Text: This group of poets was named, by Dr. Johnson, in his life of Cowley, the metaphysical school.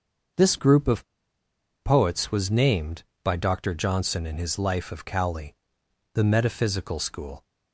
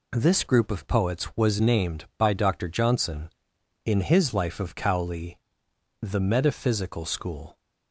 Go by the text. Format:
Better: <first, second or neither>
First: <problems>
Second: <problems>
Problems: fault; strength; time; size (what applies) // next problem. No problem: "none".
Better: second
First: starts louder than the rest; until 2.1 s; 6.5 dB // pauses between "of" and "poets"; noticeable; at 1.0 s; 0.77 s long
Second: none